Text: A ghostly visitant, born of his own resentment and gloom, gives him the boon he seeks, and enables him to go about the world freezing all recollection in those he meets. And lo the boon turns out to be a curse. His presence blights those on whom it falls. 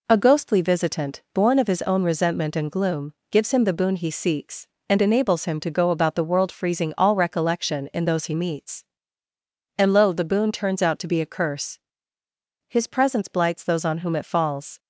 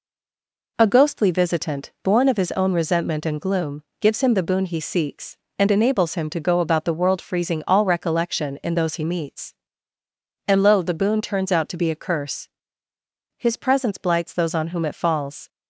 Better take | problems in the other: first | stays silent before the first word; slight; until 0.7 s; 0.7 s long

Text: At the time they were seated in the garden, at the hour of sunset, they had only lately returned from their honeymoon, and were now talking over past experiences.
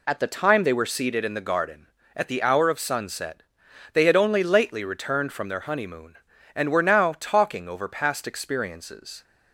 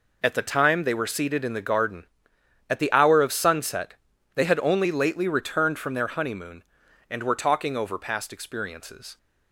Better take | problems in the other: first | skips "now"; at 7.3 s

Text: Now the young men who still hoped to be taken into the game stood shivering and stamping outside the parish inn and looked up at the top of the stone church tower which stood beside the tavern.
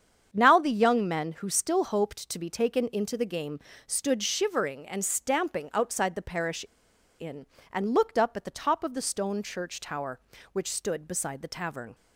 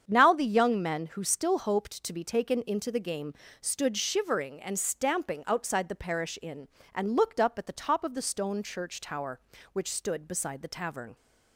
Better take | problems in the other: second | starts louder than the rest; strong; until 1.3 s; 7.5 dB; strong in the second // pauses between "game" and "stood"; slight; at 3.5 s; 0.26 s long; slight in the second // pauses between "parish" and "inn"; noticeable; at 6.6 s; 0.57 s long

